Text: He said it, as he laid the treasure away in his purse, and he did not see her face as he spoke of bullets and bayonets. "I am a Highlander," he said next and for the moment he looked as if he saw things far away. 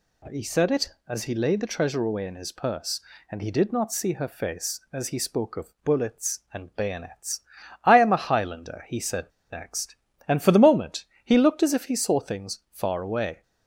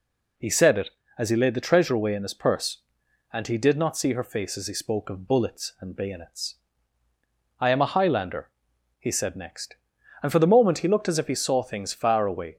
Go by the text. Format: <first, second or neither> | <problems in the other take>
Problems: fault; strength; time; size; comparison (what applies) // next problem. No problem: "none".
second | pauses between "said" and "next"; slight; at 9.2 s; 0.24 s long // pauses between "moment" and "he"; slight; at 11.0 s; 0.20 s long